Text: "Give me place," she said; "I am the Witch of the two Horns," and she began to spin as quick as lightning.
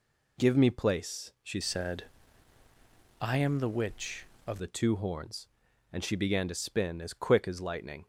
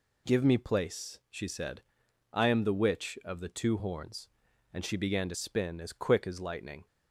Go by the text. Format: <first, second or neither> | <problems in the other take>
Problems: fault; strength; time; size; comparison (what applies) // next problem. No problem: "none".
second | changes voice from "said" to "of"; from 1.6 to 4.5 s; 2.9 s long